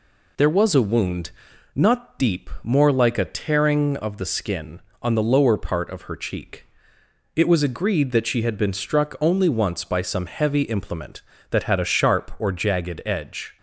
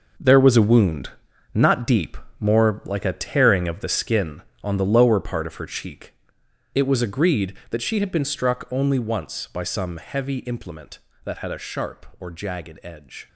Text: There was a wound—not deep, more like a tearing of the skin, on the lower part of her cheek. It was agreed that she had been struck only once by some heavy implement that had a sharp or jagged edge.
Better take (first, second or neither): first